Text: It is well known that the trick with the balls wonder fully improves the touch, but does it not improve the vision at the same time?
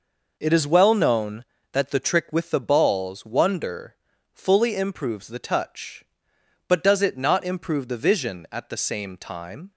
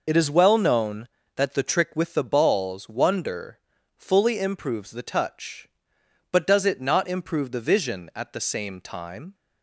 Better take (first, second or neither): first